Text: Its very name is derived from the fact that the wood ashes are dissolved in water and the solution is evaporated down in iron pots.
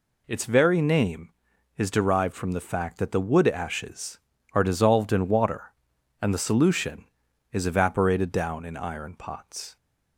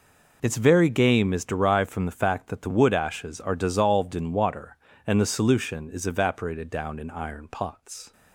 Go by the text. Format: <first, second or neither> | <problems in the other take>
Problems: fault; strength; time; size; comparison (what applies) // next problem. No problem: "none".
first | says "game" for "name"; at 0.8 s